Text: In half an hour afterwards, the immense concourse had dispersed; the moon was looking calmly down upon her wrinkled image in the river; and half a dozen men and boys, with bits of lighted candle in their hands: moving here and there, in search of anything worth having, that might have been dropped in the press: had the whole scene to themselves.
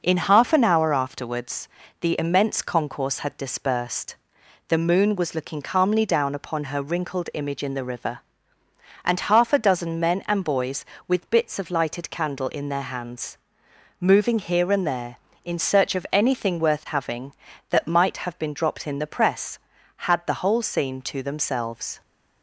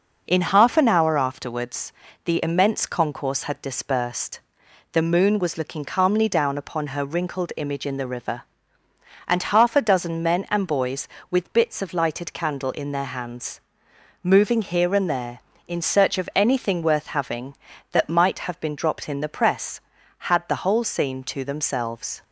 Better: neither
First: none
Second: none

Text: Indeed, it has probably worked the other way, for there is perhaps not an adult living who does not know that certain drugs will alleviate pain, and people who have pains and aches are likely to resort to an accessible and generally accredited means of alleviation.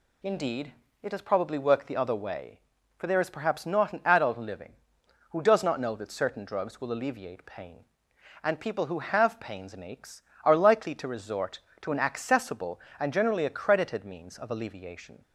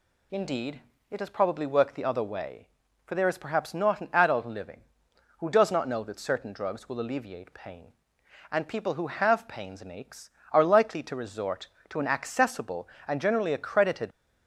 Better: first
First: none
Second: stops before "means of alleviation"; at 14.1 s

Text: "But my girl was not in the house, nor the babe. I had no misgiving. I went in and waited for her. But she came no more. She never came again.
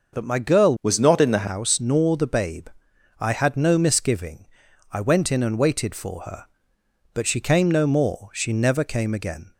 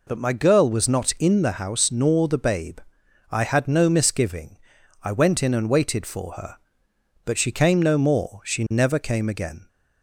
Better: second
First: changes voice from "was" to "the"; from 0.8 to 1.4 s; 0.6 s long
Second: none

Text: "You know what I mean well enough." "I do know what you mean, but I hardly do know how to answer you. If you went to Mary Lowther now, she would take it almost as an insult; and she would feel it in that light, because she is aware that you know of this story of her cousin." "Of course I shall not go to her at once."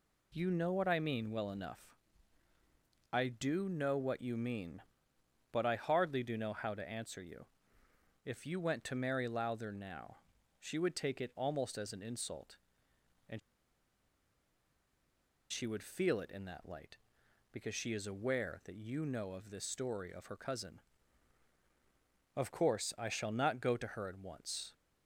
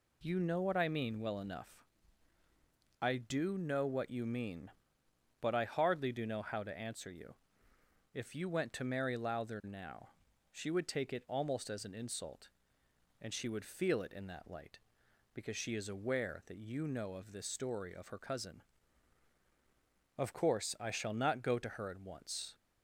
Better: second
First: pauses between "and" and "she"; strong; at 13.3 s; 2.1 s long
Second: none

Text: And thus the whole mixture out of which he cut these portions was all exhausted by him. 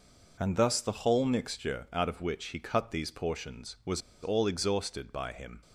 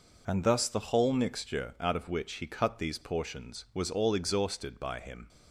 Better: second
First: pauses between "was" and "all"; slight; at 4.0 s; 0.22 s long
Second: none

